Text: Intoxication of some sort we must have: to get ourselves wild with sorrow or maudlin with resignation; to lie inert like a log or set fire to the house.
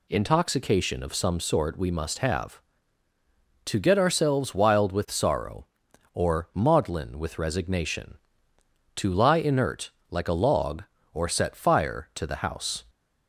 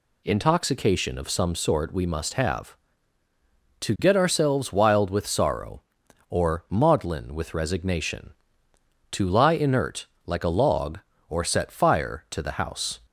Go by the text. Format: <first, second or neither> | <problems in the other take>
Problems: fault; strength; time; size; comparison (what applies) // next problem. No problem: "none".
neither | pauses between "inert" and "like"; slight; the same in both